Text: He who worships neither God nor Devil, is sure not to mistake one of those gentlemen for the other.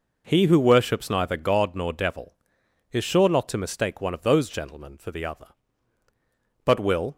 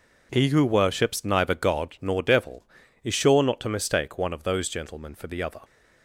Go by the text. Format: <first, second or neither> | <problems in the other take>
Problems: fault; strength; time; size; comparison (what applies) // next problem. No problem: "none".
second | goes on to say "But will"; from 6.6 s on; 0.50 s long